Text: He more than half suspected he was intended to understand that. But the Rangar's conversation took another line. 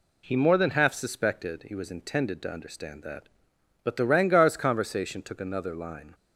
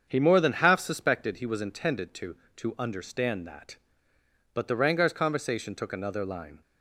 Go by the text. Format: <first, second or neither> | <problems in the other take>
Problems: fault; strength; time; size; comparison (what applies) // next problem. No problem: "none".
first | starts louder than the rest; strong; until 1.0 s; 7 dB // says "to" twice; at 2.5 s